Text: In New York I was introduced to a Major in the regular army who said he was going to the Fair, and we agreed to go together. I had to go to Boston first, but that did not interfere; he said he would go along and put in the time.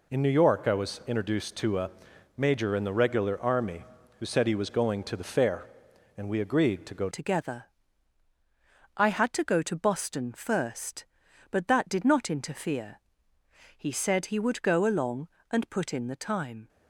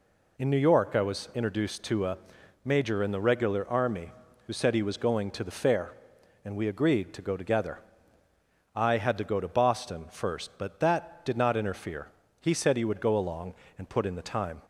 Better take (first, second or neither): second